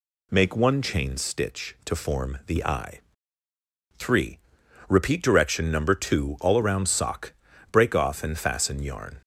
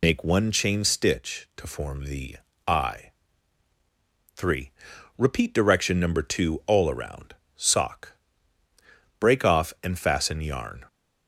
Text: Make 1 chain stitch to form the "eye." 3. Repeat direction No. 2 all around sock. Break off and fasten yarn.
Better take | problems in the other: first | loses the start of "Make"; at 0.0 s; 50 ms // pauses between "the" and "eye"; slight; at 2.3 s; 0.32 s long // pauses between "around" and "sock"; slight; at 7.3 s; 0.22 s long

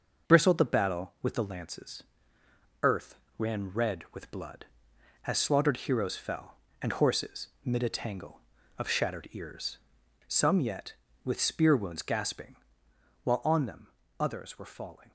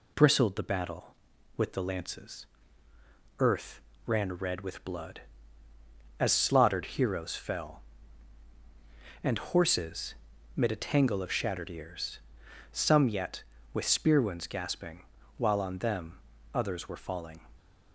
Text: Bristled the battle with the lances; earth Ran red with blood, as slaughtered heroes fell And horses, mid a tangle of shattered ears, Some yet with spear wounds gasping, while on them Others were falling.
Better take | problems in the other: neither | pauses between "earth" and "Ran"; slight; the same in both // pauses between "them" and "Others"; slight; the same in both

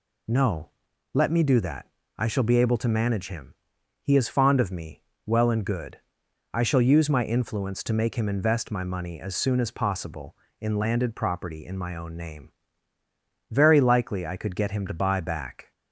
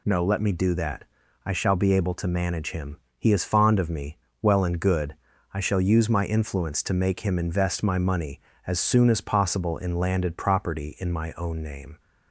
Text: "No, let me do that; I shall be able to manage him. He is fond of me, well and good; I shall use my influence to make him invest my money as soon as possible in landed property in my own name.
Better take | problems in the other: second | goes on to say "Very likely I could get him to buy back"; strong; from 13.4 s on; 2.2 s long

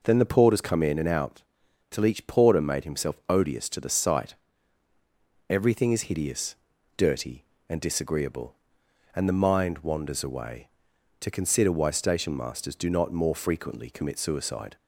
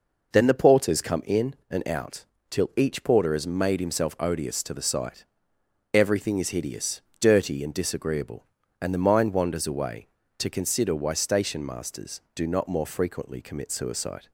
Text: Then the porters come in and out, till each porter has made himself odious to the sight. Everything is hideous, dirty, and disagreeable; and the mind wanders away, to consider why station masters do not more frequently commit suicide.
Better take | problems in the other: second | skips "has"; at 2.5 s

